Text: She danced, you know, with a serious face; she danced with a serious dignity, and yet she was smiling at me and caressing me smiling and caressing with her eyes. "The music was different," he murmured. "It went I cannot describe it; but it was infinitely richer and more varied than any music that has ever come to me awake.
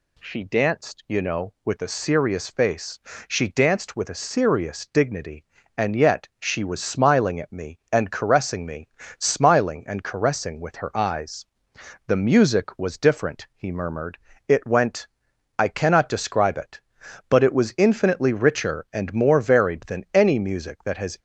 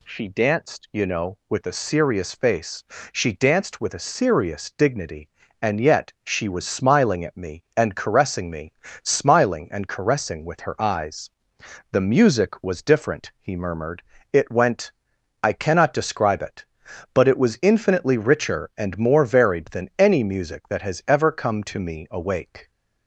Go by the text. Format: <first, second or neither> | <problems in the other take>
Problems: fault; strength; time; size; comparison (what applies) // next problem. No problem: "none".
second | pauses between "me" and "smiling"; slight; at 8.8 s; 0.30 s long; slight in the second // pauses between "went" and "I"; noticeable; at 15.0 s; 0.52 s long; noticeable in the second // stops before "ever come to me awake"; at 21.1 s